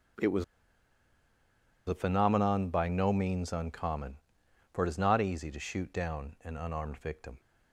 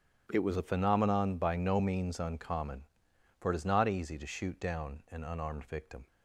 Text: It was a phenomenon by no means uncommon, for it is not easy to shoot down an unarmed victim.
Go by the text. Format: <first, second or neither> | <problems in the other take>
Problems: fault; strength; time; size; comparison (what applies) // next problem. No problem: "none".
second | starts louder than the rest; strong; until 2.6 s; 9.5 dB; strong in the second // pauses between "was" and "a"; strong; at 0.4 s; 1.4 s long